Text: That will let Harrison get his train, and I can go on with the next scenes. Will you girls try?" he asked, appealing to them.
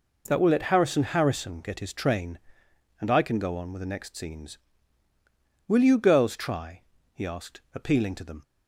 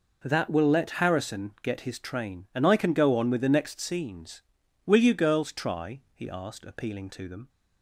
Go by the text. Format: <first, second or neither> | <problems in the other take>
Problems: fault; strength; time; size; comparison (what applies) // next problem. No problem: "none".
second | says "Harrison" twice; at 1.0 s